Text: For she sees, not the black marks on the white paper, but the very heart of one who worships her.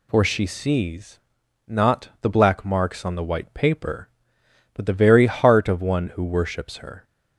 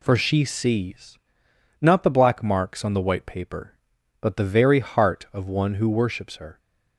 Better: neither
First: none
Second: none

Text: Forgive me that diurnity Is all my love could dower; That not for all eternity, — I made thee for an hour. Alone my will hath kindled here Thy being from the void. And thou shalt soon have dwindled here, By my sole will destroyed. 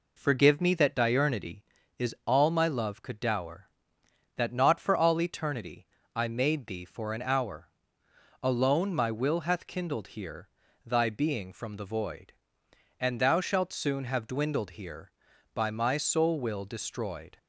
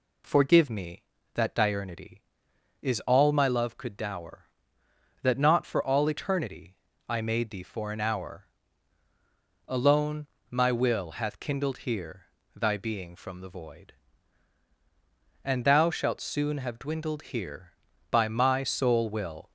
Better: first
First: pauses between "here" and "Thy"; slight; at 10.4 s; 0.36 s long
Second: pauses between "Alone" and "my"; slight; at 10.2 s; 0.24 s long // pauses between "here" and "Thy"; slight; at 12.2 s; 0.30 s long // stops before "destroyed"; at 19.4 s

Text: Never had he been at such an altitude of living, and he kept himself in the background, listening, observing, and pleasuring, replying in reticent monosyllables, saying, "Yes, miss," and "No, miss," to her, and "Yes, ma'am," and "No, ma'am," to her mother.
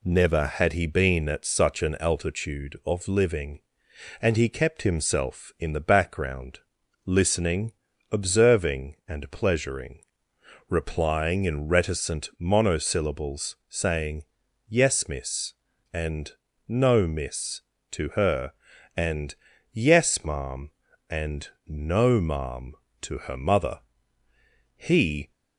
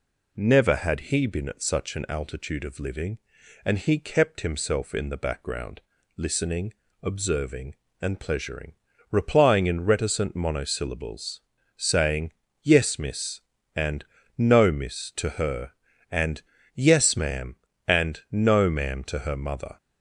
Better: second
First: pauses between "and" and "No"; slight; at 16.3 s; 0.36 s long // pauses between "and" and "Yes"; slight; at 19.3 s; 0.36 s long // pauses between "and" and "No"; slight; at 21.4 s; 0.20 s long // goes on to say "He"; from 24.7 s on; 0.56 s long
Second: pauses between "and" and "No"; slight; at 14.0 s; 0.32 s long // pauses between "and" and "Yes"; slight; at 16.4 s; 0.34 s long

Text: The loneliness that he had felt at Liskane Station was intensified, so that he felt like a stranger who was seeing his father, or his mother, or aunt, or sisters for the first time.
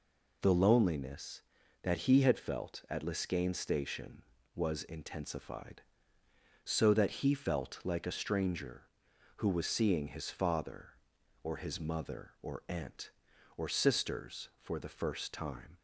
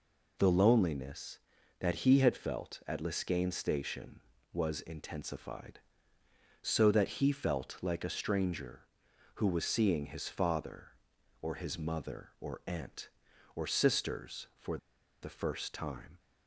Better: first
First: none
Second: pauses between "for" and "the"; at 14.7 s; 0.45 s long

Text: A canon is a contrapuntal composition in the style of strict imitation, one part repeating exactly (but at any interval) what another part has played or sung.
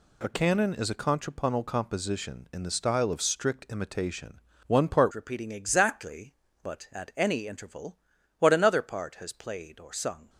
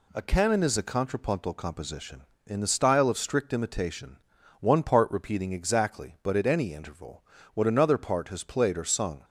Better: second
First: changes voice at "repeating"; from 5.1 s on; 5.1 s long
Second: none

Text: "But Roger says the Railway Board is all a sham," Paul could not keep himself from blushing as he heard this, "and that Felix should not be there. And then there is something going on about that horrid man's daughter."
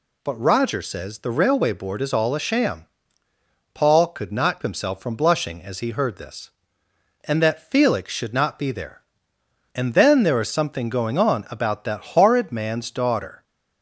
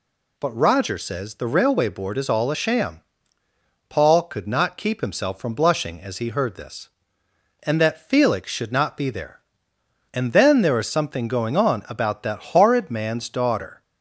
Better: second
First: skips "keep"; at 4.6 s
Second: none

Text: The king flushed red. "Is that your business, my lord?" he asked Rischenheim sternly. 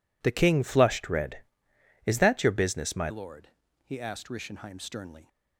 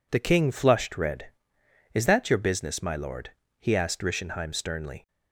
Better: second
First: changes voice at "lord"; from 3.0 s on; 2.2 s long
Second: none

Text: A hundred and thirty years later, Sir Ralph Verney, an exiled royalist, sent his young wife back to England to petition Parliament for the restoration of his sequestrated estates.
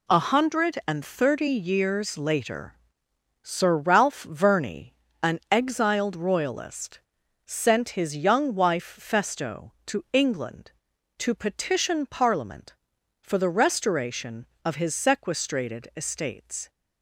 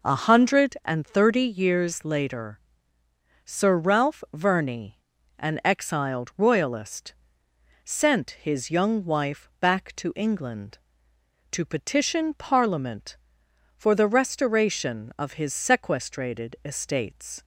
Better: second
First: says "festo" for "back"; at 9.0 s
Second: none

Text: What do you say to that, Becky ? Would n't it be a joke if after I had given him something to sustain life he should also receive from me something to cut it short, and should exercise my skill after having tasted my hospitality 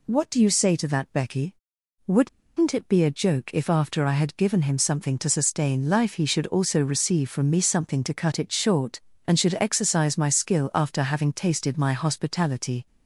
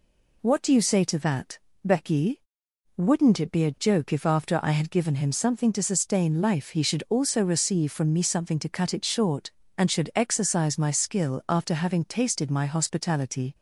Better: second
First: pauses between "Would" and "n't"; slight; at 2.2 s; 0.28 s long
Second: none

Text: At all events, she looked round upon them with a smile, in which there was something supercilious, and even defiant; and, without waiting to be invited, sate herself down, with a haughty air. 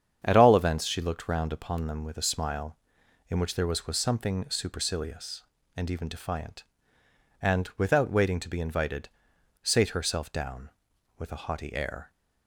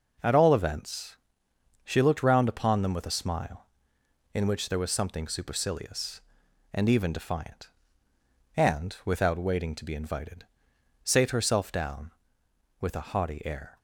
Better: second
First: starts louder than the rest; strong; until 1.2 s; 8 dB // says "was" twice; at 3.8 s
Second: none

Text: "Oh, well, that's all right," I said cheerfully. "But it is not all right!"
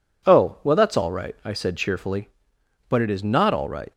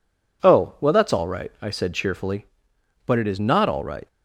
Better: neither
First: none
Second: none

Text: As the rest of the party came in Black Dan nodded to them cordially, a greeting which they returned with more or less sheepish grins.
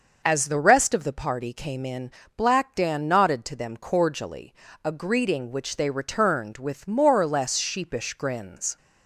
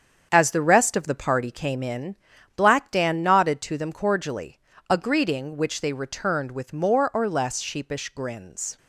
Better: first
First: pauses between "in" and "Black"; slight; at 2.0 s; 0.28 s long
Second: gets quieter; strong; throughout; 7 dB // pauses between "in" and "Black"; at 2.1 s; 0.40 s long

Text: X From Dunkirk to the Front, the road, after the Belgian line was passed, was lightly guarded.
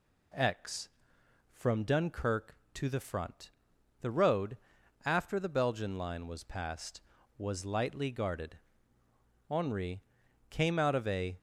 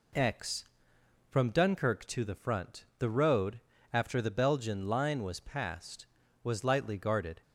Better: second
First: goes on to say "Henri came out of a"; strong; from 9.5 s on; 1.8 s long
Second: none

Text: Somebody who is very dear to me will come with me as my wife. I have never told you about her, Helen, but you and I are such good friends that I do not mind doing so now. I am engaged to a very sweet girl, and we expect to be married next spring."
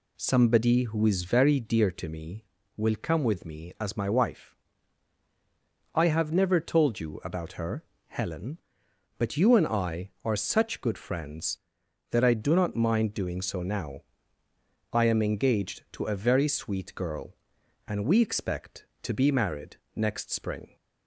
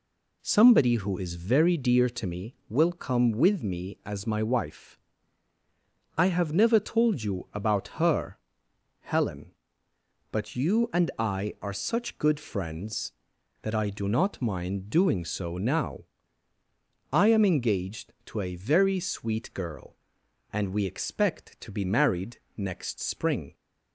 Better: neither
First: pauses between "married" and "next"; slight; at 19.7 s; 0.20 s long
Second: pauses between "married" and "next"; slight; at 22.3 s; 0.18 s long

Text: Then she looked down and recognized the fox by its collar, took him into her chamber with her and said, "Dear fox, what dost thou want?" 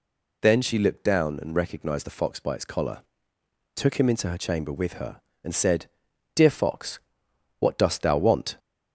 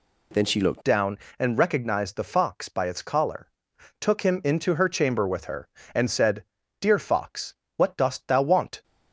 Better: first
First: none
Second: changes voice at "down"; from 0.8 s on; 8.0 s long

